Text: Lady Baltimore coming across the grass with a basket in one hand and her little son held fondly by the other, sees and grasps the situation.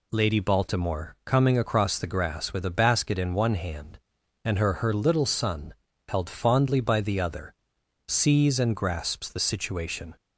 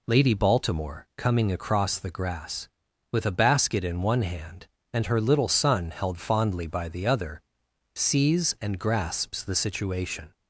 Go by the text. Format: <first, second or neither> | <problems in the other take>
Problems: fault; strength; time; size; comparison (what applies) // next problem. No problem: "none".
second | says "her" twice; at 4.7 s // pauses between "son" and "held"; slight; at 5.7 s; 0.36 s long